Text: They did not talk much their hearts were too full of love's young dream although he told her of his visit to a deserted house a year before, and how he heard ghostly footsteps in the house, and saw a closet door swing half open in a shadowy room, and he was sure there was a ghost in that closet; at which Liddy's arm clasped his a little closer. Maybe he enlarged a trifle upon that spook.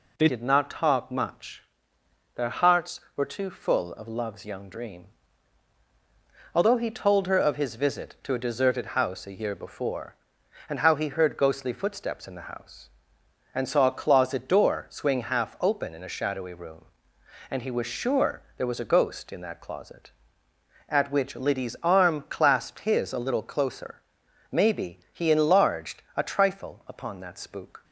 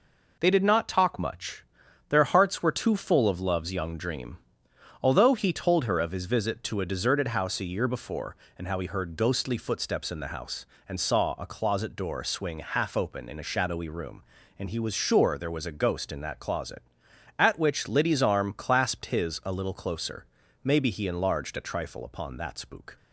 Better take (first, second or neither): second